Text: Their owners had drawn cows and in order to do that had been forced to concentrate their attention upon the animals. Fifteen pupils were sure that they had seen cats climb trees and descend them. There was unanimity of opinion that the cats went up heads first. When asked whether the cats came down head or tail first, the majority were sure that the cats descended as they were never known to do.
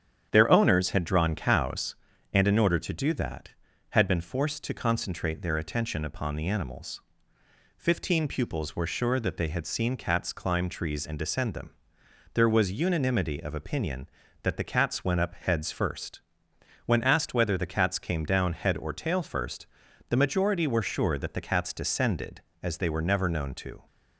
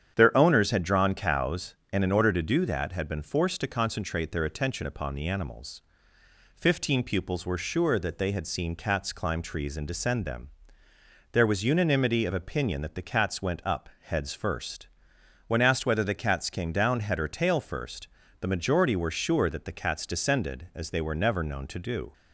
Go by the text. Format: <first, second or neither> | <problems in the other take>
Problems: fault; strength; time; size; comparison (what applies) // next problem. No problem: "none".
second | starts louder than the rest; strong; until 1.3 s; 9 dB; strong in the second // stops before "do"; at 23.8 s